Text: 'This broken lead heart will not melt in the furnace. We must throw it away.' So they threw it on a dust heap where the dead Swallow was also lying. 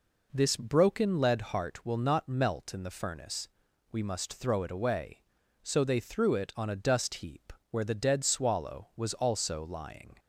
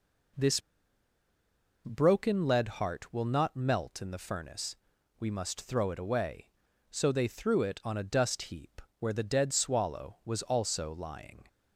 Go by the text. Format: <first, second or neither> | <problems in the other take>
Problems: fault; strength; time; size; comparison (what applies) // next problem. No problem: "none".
first | pauses between "This" and "broken"; strong; at 0.5 s; 1.2 s long // pauses between "heap" and "where"; slight; at 8.8 s; 0.18 s long; slight in the first